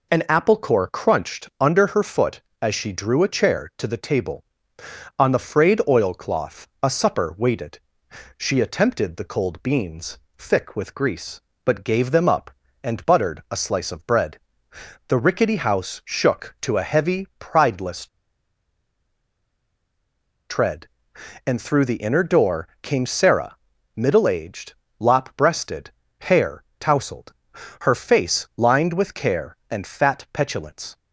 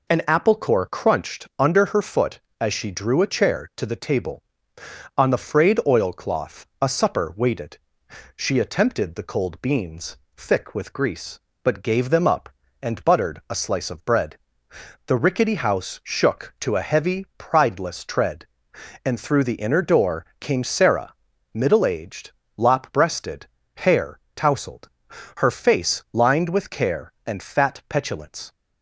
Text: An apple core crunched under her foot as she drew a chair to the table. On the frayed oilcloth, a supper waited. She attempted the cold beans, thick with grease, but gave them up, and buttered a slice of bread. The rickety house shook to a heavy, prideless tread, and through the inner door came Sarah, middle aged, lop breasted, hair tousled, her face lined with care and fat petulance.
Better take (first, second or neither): second